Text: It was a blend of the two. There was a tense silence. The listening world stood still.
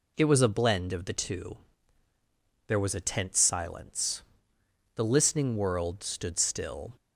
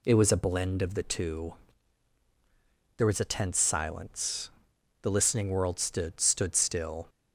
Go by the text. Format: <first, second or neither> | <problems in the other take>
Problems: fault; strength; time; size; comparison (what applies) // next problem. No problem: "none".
first | says "stood" twice; at 6.1 s